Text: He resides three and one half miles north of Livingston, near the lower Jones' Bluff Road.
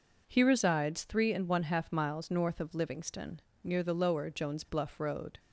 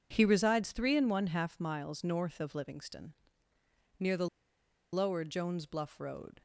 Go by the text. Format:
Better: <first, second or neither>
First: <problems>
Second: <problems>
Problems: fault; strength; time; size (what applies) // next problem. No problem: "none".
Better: first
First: none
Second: pauses between "the" and "lower"; noticeable; at 4.2 s; 0.65 s long